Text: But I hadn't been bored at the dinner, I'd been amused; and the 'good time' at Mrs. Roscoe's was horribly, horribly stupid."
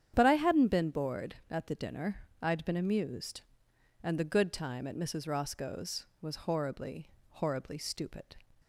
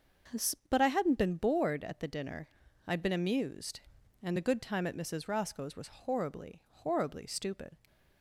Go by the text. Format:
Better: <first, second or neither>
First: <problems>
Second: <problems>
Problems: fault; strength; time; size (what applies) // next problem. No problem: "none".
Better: neither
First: starts louder than the rest; strong; until 1.1 s; 9 dB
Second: starts louder than the rest; strong; until 1.6 s; 7.5 dB